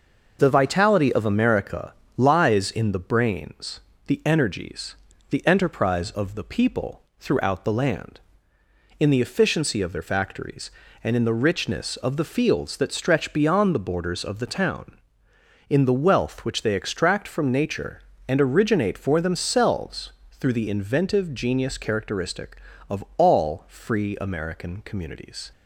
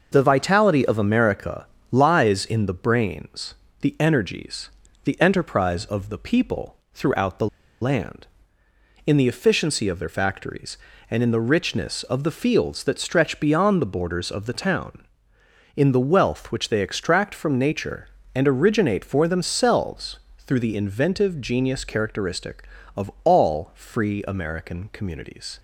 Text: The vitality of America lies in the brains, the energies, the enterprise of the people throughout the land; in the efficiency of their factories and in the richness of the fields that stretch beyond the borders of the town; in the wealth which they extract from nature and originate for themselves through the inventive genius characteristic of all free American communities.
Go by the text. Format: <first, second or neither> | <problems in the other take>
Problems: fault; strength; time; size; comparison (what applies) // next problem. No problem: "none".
first | pauses between "America" and "lies"; slight; at 1.6 s; 0.26 s long; slight in the first // pauses between "people" and "throughout"; slight; at 6.7 s; 0.16 s long; slight in the first // pauses between "the" and "land"; slight; at 7.4 s; 0.34 s long // pauses between "themselves" and "through"; slight; at 20.1 s; 0.18 s long; slight in the first